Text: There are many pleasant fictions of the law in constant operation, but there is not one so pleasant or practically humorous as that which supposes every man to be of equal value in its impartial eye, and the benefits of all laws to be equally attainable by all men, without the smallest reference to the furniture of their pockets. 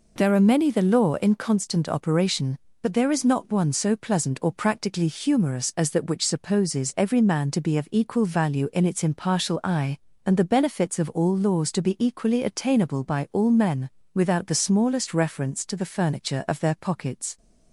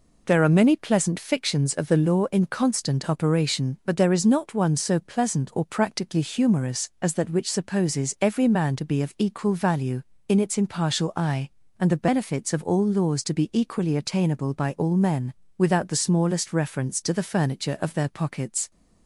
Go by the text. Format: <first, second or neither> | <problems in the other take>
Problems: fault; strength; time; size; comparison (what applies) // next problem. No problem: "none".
second | skips "pleasant fictions of"; at 0.7 s